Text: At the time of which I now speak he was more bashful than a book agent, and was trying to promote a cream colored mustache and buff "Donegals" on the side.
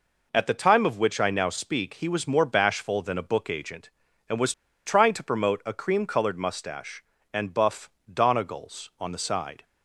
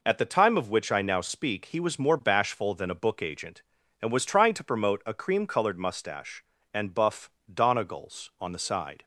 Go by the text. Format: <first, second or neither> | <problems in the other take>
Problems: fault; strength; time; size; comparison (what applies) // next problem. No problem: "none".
second | pauses between "was" and "trying"; slight; at 4.5 s; 0.32 s long // pauses between "buff" and "Donegals"; slight; at 7.8 s; 0.18 s long; slight in the second